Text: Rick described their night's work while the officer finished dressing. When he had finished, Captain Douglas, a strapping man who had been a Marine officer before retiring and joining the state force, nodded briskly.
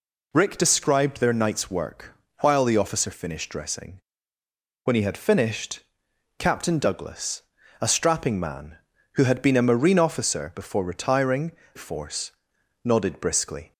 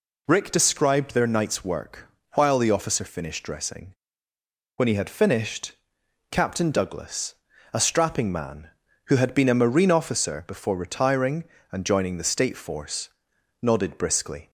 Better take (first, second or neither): second